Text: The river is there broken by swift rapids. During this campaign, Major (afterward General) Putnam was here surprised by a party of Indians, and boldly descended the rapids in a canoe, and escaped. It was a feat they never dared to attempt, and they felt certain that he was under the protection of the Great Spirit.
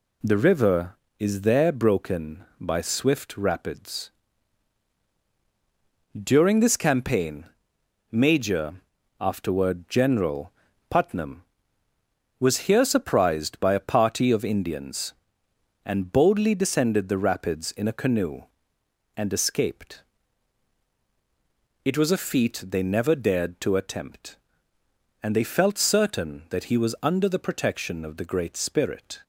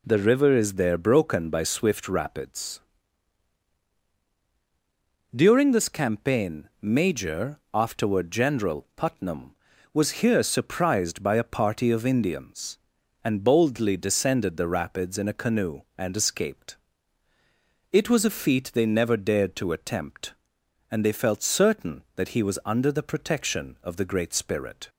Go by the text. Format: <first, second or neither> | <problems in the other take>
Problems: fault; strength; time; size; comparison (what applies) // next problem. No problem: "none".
neither | none